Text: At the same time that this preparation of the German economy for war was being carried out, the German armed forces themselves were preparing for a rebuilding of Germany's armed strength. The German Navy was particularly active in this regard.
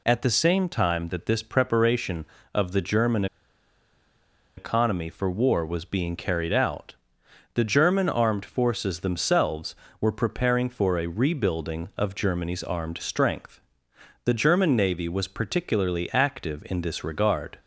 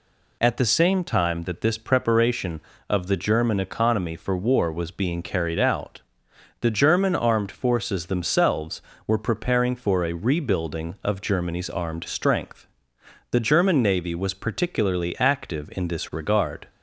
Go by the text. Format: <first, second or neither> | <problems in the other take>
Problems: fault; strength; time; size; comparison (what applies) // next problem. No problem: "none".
second | pauses between "German" and "economy"; strong; at 3.2 s; 1.3 s long